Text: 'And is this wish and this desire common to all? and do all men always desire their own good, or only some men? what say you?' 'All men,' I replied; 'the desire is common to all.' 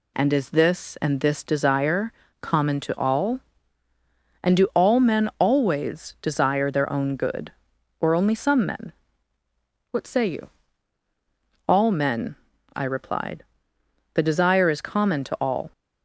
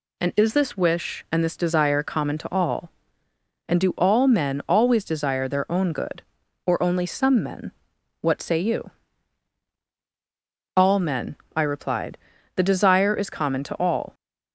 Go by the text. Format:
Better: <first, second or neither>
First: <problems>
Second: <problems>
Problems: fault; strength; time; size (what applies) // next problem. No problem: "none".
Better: second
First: skips "wish"; at 0.9 s // pauses between "desire" and "common"; slight; at 2.1 s; 0.30 s long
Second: none